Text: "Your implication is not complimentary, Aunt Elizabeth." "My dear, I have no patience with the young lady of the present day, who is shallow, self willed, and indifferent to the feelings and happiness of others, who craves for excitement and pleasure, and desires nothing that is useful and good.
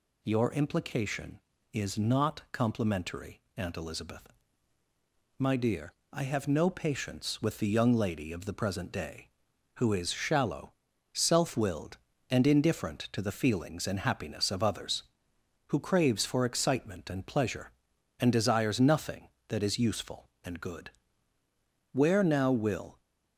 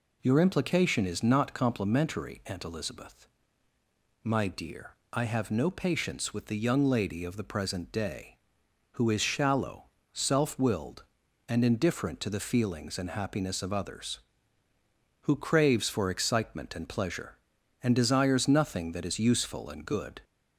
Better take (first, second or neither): second